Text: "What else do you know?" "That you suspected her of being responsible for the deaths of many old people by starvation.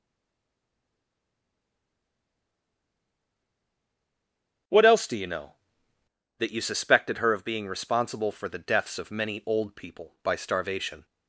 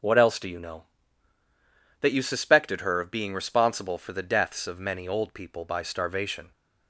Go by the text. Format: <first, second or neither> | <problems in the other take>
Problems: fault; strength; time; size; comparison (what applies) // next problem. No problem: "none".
second | stays silent before the first word; strong; until 4.6 s; 4.6 s long // starts louder than the rest; until 6.5 s; 7 dB